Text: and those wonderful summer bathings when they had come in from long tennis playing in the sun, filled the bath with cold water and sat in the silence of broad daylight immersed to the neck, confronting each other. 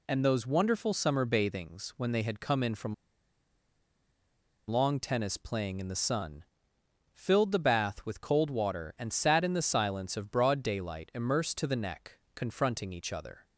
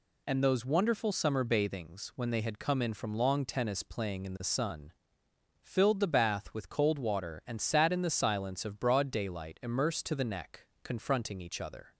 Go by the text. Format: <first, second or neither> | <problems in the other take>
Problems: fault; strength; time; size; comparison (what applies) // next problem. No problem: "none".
second | pauses between "from" and "long"; strong; at 2.9 s; 1.7 s long